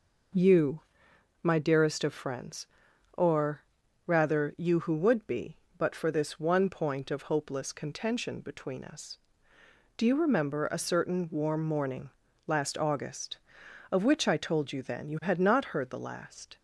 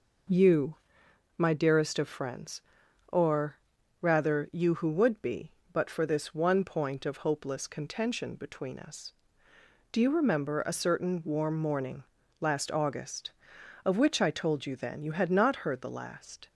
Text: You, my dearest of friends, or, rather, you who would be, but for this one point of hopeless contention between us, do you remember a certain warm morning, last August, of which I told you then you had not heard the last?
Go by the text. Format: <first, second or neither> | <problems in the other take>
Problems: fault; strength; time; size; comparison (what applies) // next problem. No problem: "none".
neither | none